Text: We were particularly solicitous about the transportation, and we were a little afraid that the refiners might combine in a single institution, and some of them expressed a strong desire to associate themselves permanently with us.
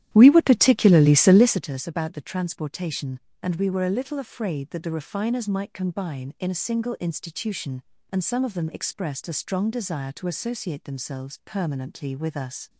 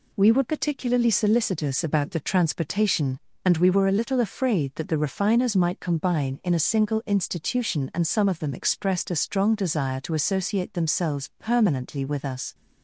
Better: second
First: starts louder than the rest; strong; until 1.8 s; 12.5 dB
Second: none

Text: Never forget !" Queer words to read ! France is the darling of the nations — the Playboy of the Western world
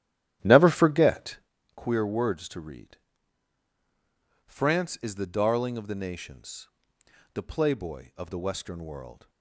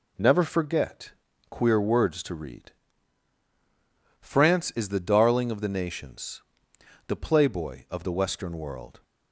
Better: second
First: starts louder than the rest; strong; until 1.5 s; 11.5 dB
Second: none

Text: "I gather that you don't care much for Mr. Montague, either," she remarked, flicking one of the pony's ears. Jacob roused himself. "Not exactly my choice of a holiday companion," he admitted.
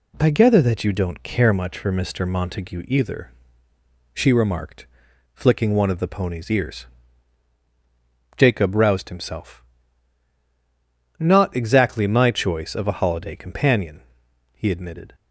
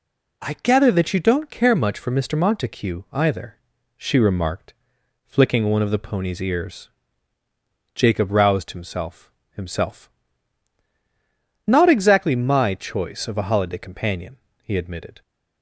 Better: first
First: none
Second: says "himself" twice; at 9.5 s

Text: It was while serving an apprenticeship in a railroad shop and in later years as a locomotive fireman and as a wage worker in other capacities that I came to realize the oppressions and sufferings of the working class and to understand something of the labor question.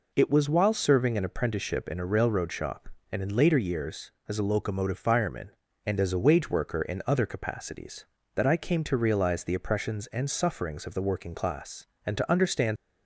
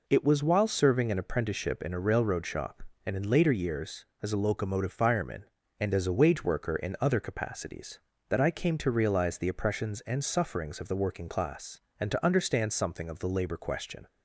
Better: second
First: stops before "something of the labor question"; at 12.7 s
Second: none

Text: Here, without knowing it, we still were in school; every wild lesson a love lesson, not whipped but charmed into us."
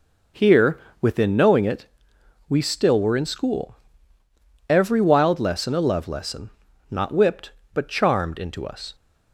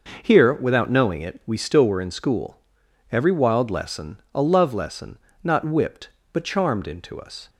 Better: second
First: says "within" for "without"; at 1.0 s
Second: none

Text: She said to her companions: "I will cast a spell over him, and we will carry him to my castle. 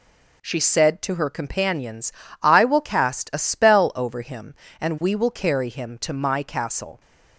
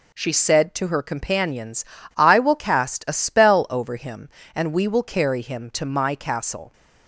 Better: neither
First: none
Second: none

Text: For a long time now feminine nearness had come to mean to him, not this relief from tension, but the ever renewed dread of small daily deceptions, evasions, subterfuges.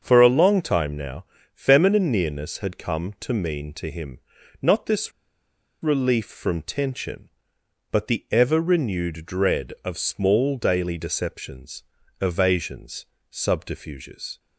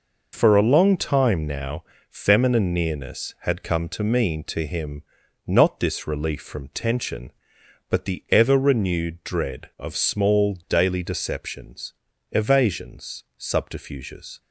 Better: second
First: starts louder than the rest; until 1.0 s; 6.5 dB // pauses between "now" and "feminine"; slight; at 1.2 s; 0.30 s long // pauses between "this" and "relief"; noticeable; at 5.1 s; 0.71 s long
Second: pauses between "now" and "feminine"; slight; at 1.8 s; 0.26 s long

